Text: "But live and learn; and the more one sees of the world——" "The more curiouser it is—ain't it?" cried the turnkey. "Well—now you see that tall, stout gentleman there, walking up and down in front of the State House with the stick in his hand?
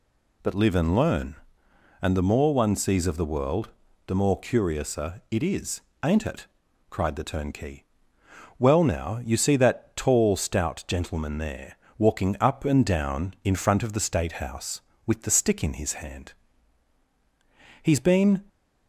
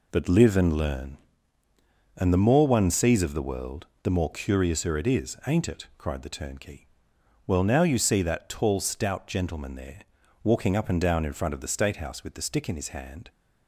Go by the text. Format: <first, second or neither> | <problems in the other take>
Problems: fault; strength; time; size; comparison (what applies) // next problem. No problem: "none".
second | goes on to say "He's been"; noticeable; from 17.8 s on; 0.62 s long